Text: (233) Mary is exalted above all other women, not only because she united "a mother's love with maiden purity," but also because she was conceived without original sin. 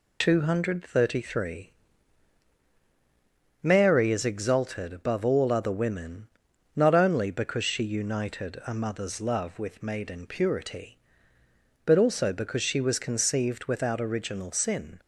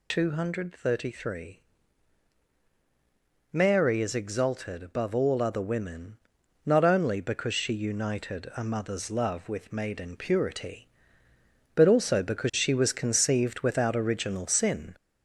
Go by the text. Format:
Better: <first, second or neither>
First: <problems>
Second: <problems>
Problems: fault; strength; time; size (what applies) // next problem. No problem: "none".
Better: first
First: none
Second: gets louder; throughout; 3.5 dB